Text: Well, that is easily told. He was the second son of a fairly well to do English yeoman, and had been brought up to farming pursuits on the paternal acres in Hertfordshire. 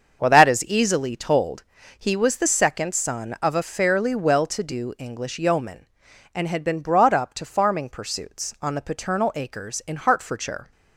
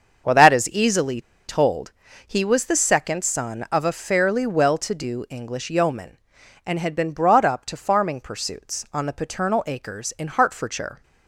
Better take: first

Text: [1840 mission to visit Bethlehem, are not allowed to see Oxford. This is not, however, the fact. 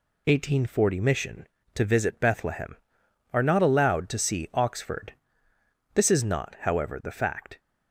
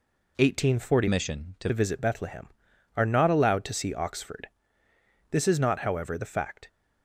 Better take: first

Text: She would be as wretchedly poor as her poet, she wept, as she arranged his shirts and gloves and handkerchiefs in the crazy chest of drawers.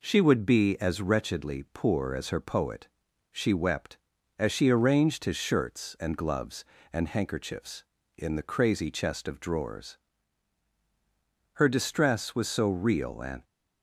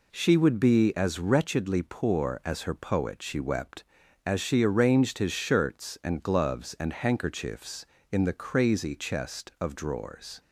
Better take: second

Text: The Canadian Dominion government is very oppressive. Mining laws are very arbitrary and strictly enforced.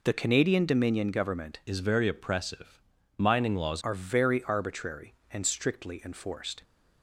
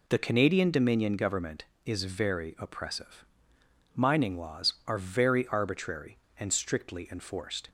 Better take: second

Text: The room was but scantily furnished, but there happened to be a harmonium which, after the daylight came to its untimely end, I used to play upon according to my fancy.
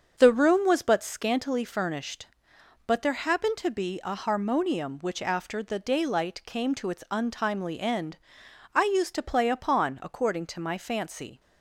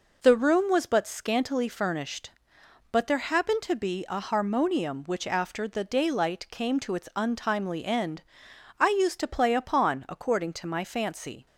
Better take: second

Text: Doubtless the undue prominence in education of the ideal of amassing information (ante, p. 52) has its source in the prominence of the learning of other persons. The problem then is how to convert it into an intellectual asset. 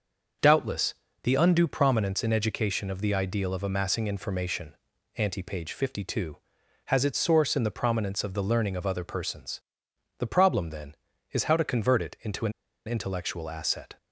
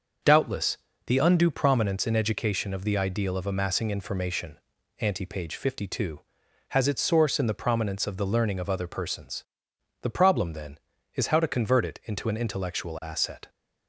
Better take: second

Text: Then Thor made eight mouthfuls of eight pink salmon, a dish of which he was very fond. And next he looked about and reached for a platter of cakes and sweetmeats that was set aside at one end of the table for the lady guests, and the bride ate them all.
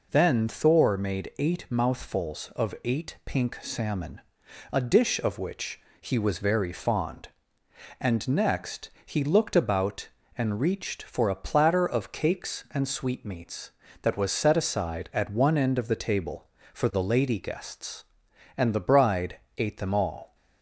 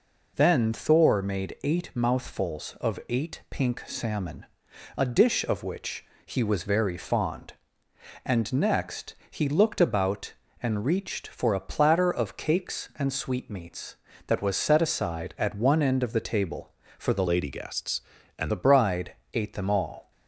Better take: first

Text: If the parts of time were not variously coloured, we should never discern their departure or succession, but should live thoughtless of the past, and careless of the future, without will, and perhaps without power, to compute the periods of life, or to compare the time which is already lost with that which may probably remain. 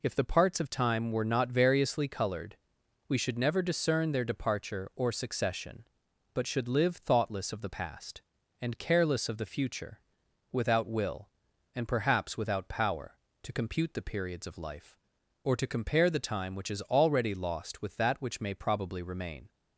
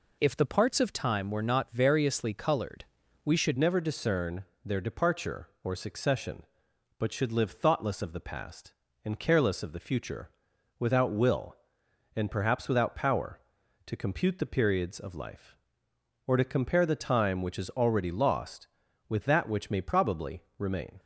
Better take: first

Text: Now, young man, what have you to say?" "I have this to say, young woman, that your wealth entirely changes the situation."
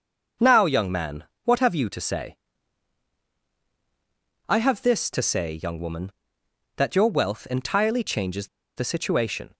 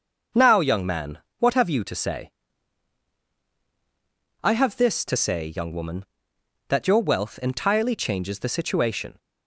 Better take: second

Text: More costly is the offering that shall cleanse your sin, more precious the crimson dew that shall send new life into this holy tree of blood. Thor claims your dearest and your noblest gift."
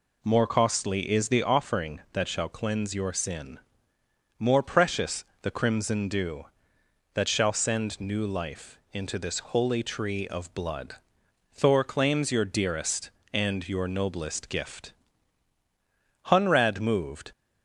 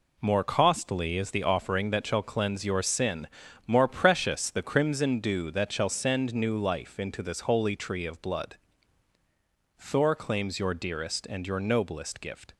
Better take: second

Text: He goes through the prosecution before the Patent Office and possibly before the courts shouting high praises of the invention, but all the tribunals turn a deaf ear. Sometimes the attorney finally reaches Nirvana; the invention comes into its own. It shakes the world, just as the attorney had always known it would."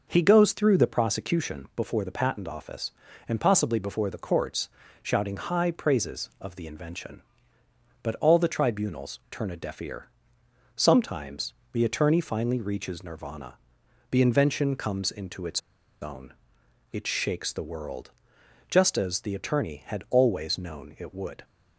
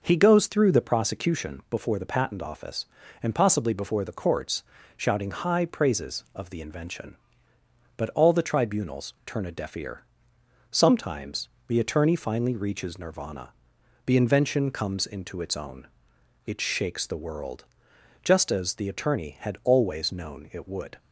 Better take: second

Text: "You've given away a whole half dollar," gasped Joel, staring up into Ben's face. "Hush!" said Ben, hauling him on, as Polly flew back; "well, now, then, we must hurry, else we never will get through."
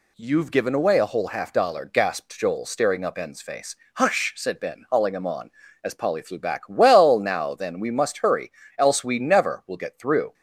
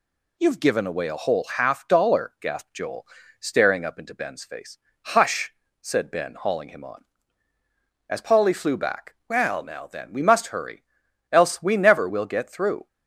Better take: second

